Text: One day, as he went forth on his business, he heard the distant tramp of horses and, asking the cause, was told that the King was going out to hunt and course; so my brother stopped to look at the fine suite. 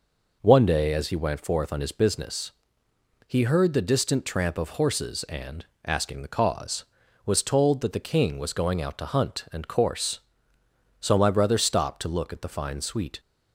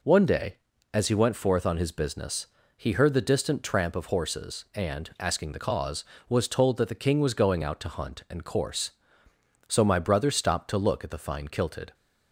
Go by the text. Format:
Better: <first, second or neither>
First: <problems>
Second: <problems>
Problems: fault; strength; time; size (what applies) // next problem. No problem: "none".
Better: first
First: none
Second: says "kilted" for "suite"; at 11.4 s